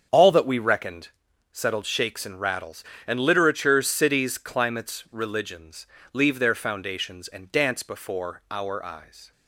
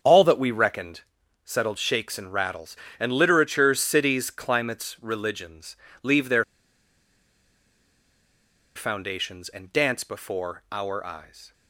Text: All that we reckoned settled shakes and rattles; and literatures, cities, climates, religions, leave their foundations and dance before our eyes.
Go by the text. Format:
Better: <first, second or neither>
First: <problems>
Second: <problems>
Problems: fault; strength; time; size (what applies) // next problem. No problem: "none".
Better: first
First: starts louder than the rest; strong; until 1.5 s; 7.5 dB // pauses between "reckoned" and "settled"; at 1.0 s; 0.42 s long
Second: starts louder than the rest; strong; until 1.4 s; 7.5 dB // pauses between "reckoned" and "settled"; at 1.0 s; 0.42 s long // pauses between "their" and "foundations"; strong; at 6.4 s; 2.3 s long